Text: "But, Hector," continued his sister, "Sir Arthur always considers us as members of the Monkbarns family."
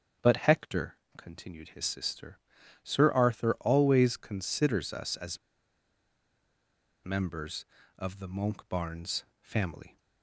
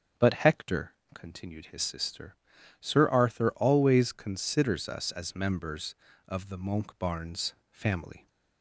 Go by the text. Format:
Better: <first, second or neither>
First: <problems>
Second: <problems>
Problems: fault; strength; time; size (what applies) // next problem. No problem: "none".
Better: second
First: starts louder than the rest; until 1.4 s; 6.5 dB // pauses between "as" and "members"; strong; at 5.3 s; 1.6 s long // pauses between "Monkbarns" and "family"; slight; at 9.2 s; 0.18 s long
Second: starts louder than the rest; until 1.3 s; 7 dB // pauses between "Monkbarns" and "family"; slight; at 7.5 s; 0.18 s long